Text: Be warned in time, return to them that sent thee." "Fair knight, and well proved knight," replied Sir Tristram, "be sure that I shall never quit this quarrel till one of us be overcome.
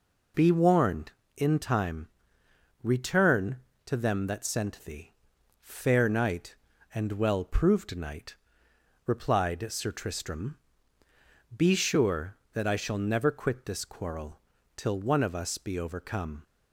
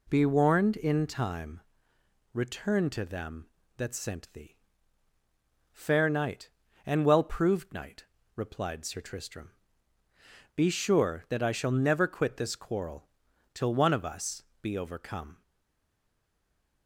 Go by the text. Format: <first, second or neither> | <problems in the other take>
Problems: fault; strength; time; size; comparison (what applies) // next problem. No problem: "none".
first | pauses between "quarrel" and "till"; at 13.0 s; 0.42 s long; slight in the first // pauses between "us" and "be"; slight; at 14.4 s; 0.18 s long // stays silent after the last word; noticeable; from 15.4 s on; 1.4 s long